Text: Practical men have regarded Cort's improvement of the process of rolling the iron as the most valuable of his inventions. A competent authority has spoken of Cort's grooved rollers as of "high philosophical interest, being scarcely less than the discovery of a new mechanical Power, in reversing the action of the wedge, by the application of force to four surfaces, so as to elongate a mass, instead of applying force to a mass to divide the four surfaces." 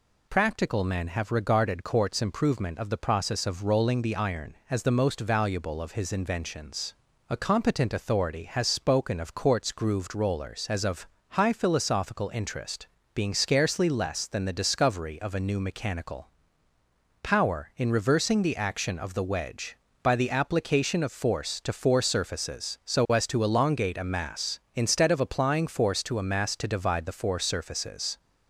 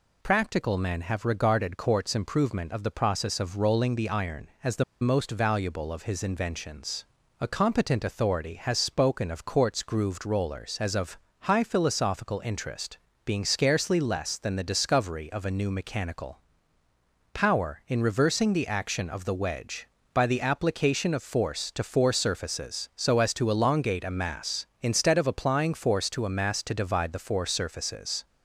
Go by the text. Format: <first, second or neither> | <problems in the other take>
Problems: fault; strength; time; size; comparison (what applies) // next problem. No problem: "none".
first | pauses between "the" and "most"; slight; at 4.8 s; 0.18 s long // pauses between "of" and "high"; slight; at 11.1 s; 0.24 s long; slight in the first // pauses between "mechanical" and "Power"; noticeable; at 16.3 s; 0.94 s long; noticeable in the first